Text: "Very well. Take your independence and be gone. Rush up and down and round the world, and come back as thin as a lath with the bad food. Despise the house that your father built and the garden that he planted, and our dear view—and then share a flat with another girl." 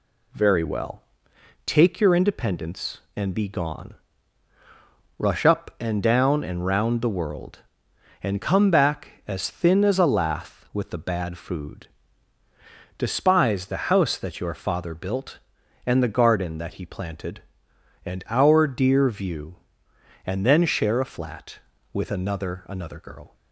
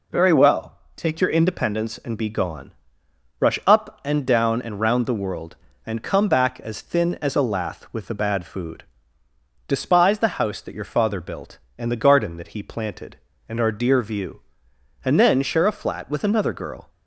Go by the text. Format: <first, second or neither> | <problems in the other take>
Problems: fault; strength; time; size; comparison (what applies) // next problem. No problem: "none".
second | says "another" twice; at 22.6 s